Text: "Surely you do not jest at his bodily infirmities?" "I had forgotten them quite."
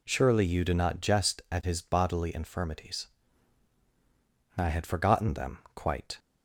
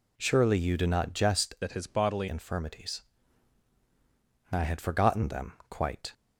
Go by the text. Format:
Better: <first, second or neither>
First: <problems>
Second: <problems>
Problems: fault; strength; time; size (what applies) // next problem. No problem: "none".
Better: first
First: none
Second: changes voice from "at" to "bodily"; from 1.6 to 2.2 s; 0.6 s long